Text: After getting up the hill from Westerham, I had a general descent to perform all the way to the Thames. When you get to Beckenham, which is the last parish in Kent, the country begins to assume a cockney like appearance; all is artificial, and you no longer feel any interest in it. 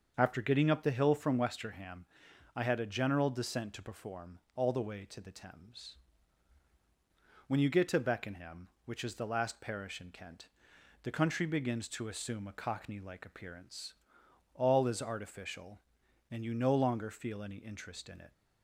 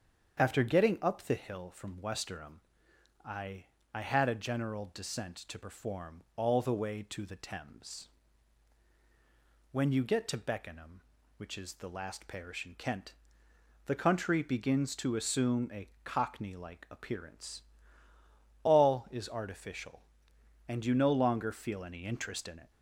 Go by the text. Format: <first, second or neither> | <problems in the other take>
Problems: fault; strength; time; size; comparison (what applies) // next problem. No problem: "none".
first | starts louder than the rest; strong; until 1.4 s; 7.5 dB; also in the first // says "I" twice; at 3.9 s // pauses between "a" and "cockney"; slight; at 15.8 s; 0.16 s long